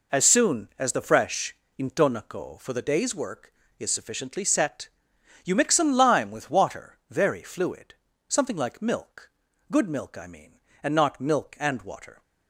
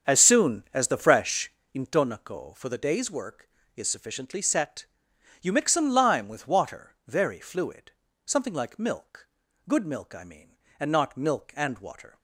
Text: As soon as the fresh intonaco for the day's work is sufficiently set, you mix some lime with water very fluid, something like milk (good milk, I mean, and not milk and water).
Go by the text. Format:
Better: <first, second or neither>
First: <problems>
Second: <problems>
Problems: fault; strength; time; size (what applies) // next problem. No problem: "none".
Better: first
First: pauses between "fresh" and "intonaco"; slight; at 1.5 s; 0.24 s long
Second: starts louder than the rest; strong; until 1.8 s; 7.5 dB // pauses between "fresh" and "intonaco"; slight; at 1.5 s; 0.24 s long